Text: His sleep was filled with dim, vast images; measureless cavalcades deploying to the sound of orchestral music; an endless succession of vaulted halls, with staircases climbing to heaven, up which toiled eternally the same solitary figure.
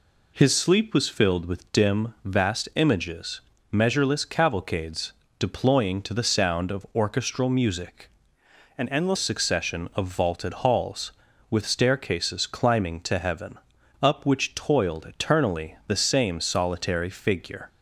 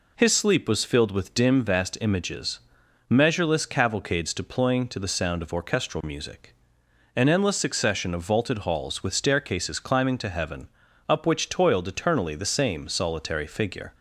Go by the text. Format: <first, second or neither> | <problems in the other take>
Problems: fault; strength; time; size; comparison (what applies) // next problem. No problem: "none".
second | pauses between "cavalcades" and "deploying"; slight; at 5.1 s; 0.26 s long // changes voice from "an" to "endless"; from 8.7 to 9.1 s; 0.4 s long